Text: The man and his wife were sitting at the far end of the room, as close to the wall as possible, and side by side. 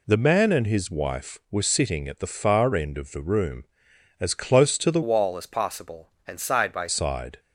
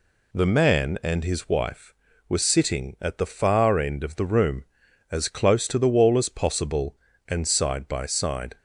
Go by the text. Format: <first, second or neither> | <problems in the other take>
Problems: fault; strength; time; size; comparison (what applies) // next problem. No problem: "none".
second | changes voice from "wall" to "by"; from 5.0 to 6.8 s; 1.8 s long